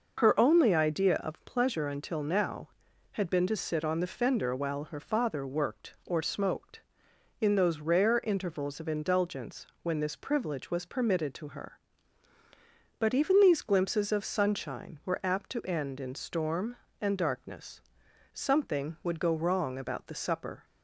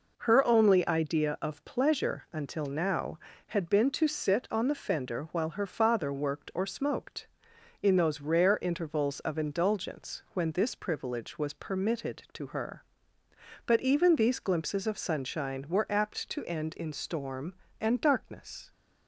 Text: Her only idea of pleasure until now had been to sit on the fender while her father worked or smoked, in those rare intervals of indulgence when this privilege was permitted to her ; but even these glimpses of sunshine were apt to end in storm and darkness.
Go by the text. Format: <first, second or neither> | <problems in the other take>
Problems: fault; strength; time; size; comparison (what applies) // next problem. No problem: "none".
second | pauses between "indulgence" and "when"; slight; at 9.6 s; 0.18 s long // goes on to say "Something would go wrong about the supper"; strong; from 18.3 s on; 2.3 s long